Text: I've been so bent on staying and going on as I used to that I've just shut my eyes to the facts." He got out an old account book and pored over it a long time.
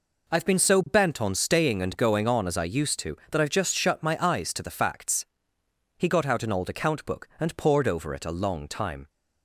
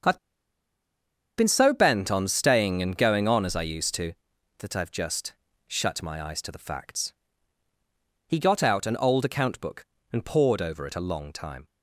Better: first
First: none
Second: starts louder than the rest; until 2.2 s; 6.5 dB // pauses between "I've" and "been"; at 0.1 s; 1.1 s long // pauses between "just" and "shut"; slight; at 5.3 s; 0.36 s long

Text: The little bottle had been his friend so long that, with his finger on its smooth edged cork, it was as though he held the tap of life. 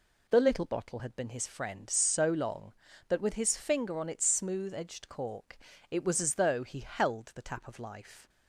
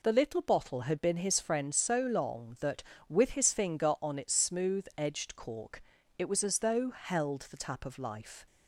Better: first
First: none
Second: skips "he"; at 6.8 s

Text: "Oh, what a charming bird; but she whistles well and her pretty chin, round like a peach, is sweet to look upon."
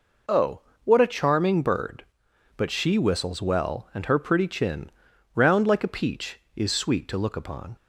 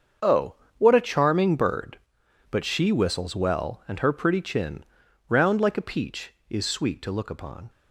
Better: first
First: none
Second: gets quieter; strong; throughout; 12.5 dB

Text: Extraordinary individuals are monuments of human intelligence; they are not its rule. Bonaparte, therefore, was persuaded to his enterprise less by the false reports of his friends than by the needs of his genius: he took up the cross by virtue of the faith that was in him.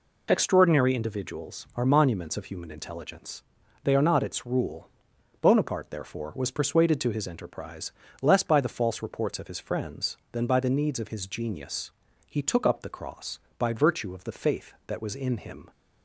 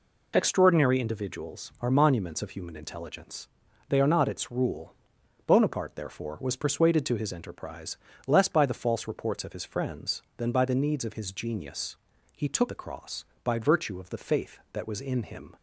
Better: first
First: pauses between "enterprise" and "less"; slight; at 7.9 s; 0.30 s long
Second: pauses between "enterprise" and "less"; slight; at 7.9 s; 0.30 s long // skips "up"; at 12.6 s

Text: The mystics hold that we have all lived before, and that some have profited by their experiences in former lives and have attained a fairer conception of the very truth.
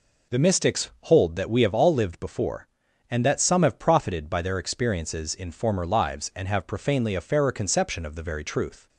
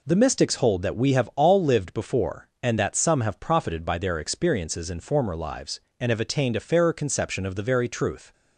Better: second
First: says "profanely" for "attained"; at 6.6 s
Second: none

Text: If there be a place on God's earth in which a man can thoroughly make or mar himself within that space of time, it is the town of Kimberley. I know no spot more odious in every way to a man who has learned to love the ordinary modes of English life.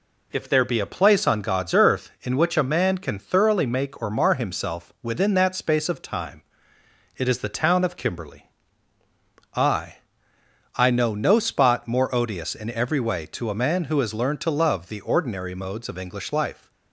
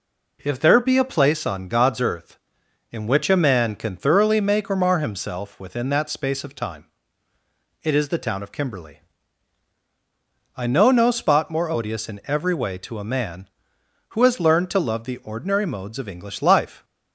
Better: second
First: says "I" twice; at 10.7 s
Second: none

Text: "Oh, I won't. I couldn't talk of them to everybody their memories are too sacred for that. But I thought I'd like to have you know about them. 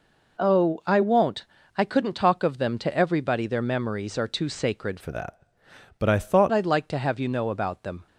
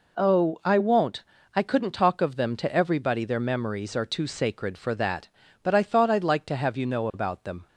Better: second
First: changes voice from "for" to "thought"; from 4.9 to 6.5 s; 1.6 s long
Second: none

